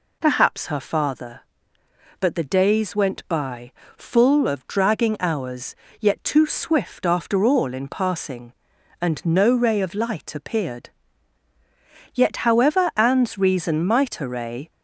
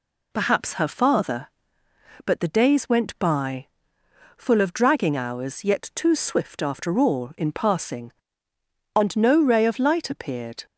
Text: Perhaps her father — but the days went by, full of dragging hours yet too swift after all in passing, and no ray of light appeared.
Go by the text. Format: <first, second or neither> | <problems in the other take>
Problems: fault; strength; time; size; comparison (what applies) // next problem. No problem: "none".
second | pauses between "hours" and "yet"; slight; at 5.7 s; 0.24 s long // goes on to say "Yet however Anne's reason might array"; strong; from 12.1 s on; 2.5 s long